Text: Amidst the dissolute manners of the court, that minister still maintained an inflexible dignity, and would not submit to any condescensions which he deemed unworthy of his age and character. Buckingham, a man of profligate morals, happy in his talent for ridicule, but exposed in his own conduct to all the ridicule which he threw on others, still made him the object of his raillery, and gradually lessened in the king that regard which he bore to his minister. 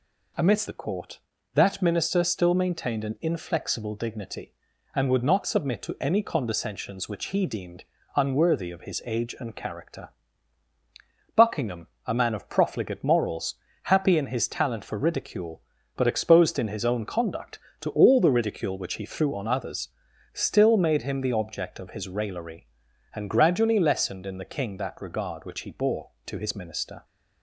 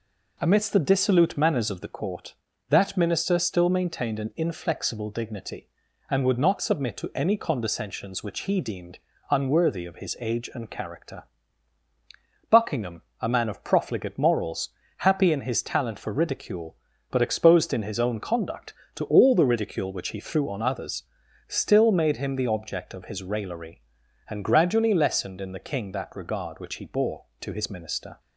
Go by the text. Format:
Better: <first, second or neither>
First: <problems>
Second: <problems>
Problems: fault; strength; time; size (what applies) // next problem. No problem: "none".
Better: second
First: skips "the dissolute manners of"; at 0.6 s // pauses between "deemed" and "unworthy"; slight; at 7.8 s; 0.32 s long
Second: pauses between "deemed" and "unworthy"; slight; at 8.9 s; 0.32 s long